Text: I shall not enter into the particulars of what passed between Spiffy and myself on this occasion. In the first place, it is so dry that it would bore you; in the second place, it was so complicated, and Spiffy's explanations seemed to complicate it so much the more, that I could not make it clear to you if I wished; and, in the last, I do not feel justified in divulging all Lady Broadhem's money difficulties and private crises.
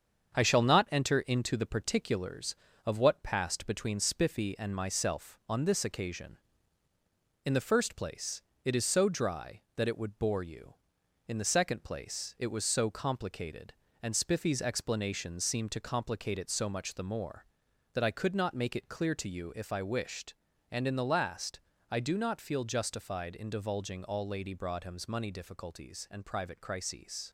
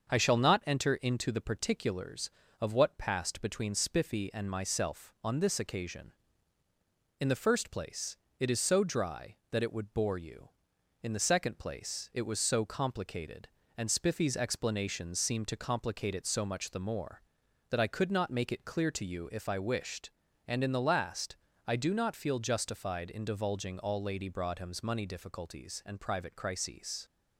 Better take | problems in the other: second | gets quieter; noticeable; throughout; 4.5 dB // starts louder than the rest; strong; until 1.3 s; 7.5 dB; also in the second

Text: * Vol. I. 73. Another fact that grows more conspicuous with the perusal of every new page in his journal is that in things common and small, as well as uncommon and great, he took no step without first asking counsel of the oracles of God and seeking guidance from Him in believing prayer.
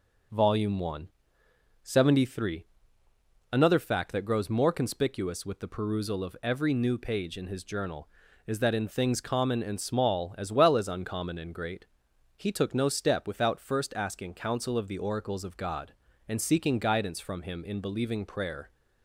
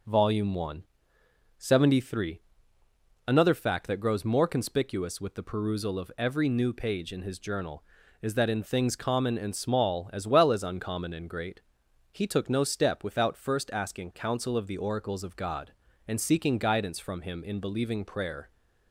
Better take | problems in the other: neither | none

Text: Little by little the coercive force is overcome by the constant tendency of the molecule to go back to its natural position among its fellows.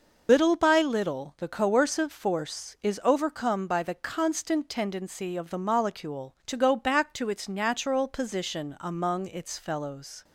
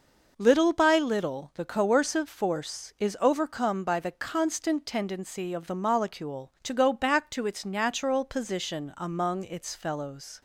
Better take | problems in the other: second | loses the start of "Little"; at 0.2 s; 95 ms

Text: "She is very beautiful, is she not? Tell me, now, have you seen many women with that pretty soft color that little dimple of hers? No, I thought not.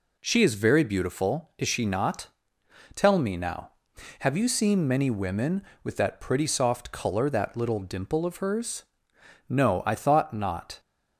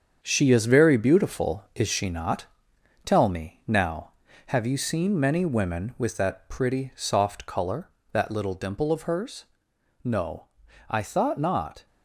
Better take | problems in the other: first | gets quieter; strong; throughout; 7.5 dB

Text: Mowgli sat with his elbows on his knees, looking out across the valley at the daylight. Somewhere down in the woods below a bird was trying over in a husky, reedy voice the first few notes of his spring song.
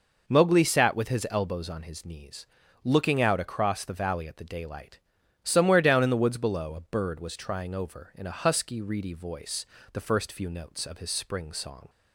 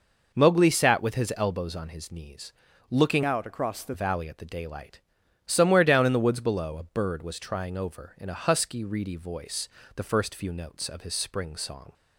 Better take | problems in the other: first | changes voice from "out" to "the"; from 3.2 to 3.9 s; 0.7 s long // pauses between "voice" and "the"; slight; at 9.6 s; 0.26 s long; slight in the first

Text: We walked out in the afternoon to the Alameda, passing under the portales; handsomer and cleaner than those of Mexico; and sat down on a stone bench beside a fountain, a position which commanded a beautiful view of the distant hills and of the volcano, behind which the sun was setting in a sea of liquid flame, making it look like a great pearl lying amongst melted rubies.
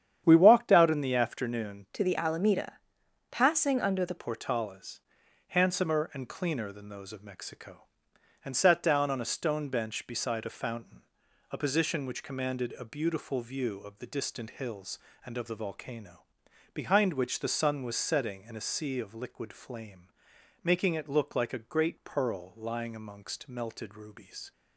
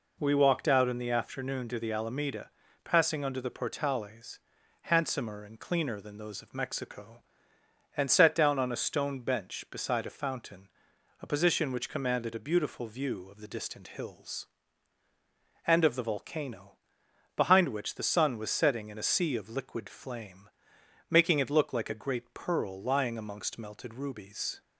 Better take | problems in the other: second | starts louder than the rest; strong; until 1.2 s; 9.5 dB // changes voice from "to" to "the"; from 1.9 to 4.1 s; 2.2 s long

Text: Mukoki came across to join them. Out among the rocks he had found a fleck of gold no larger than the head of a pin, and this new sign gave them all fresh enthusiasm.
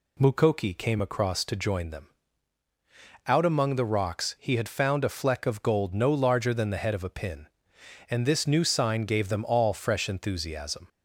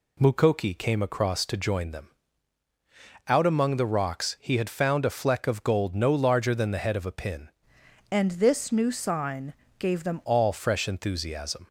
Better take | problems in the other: first | changes voice from "and" to "them"; from 8.0 to 10.2 s; 2.2 s long // pauses between "sign" and "gave"; slight; at 9.5 s; 0.26 s long

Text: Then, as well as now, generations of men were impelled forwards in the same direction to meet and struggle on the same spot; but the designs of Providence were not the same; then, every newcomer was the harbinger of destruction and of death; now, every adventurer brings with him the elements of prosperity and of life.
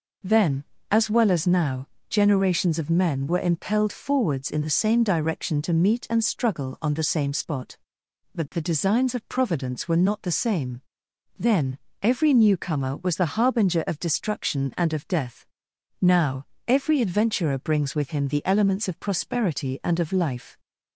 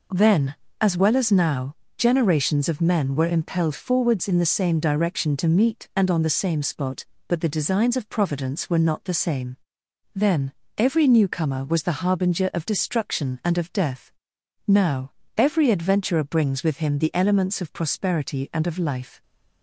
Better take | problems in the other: first | skips "struggle"; at 6.1 s

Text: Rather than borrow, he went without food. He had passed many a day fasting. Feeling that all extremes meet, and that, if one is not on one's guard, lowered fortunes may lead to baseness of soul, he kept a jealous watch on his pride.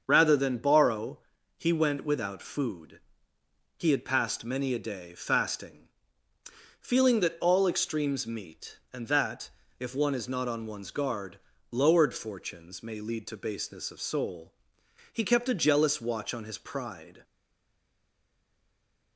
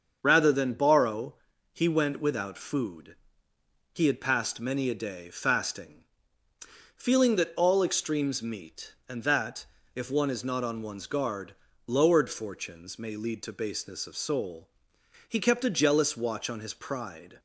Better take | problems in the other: second | starts louder than the rest; until 1.0 s; 7 dB; also in the second // stays silent after the last word; noticeable; from 17.2 s on; 1.9 s long

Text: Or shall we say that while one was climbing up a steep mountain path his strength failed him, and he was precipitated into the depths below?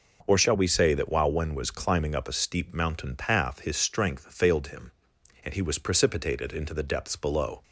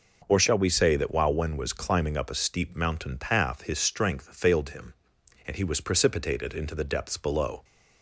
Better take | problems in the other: neither | none

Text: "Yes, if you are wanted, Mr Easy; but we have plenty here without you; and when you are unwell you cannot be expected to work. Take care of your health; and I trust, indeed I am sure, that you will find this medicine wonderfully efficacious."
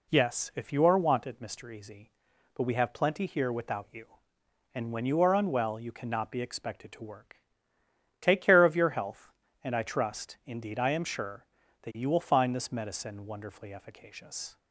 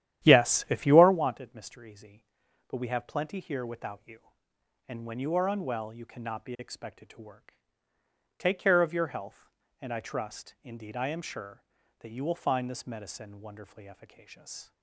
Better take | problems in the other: first | starts louder than the rest; strong; until 1.2 s; 11.5 dB

